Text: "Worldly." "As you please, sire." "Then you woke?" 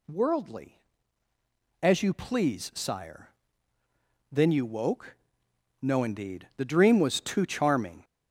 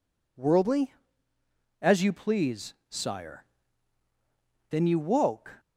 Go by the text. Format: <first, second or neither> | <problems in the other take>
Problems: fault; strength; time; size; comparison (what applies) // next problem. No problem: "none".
second | goes on to say "No indeed the dream was too charming"; strong; from 5.7 s on; 2.2 s long